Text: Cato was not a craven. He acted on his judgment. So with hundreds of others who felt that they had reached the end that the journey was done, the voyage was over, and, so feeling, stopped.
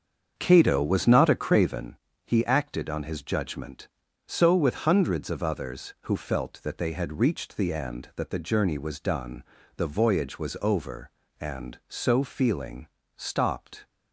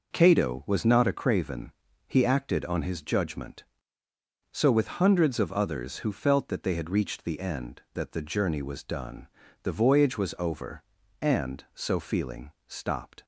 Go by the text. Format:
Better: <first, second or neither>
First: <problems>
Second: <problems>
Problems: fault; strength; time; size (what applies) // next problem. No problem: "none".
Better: second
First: starts louder than the rest; strong; until 1.9 s; 7 dB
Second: none